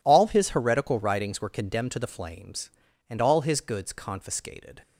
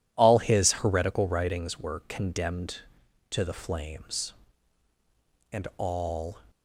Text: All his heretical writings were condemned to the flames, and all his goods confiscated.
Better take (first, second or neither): first